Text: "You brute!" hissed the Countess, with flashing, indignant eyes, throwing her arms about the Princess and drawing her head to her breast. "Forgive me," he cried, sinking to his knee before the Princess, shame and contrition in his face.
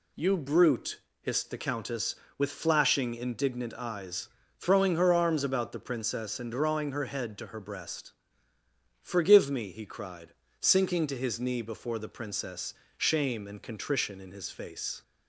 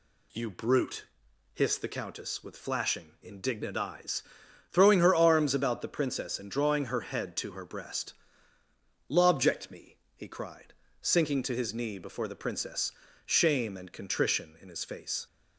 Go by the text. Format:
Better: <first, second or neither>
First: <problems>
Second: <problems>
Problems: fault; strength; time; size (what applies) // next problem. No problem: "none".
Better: first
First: none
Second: says "Lobject" for "Forgive"; at 9.0 s